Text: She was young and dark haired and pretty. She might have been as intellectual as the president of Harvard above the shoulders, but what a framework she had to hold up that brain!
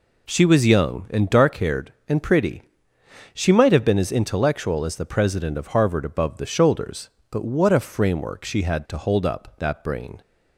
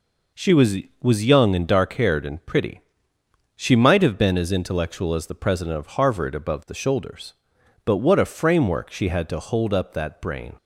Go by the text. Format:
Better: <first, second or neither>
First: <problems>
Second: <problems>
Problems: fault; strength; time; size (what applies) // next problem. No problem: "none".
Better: first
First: none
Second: says "was" twice; at 1.0 s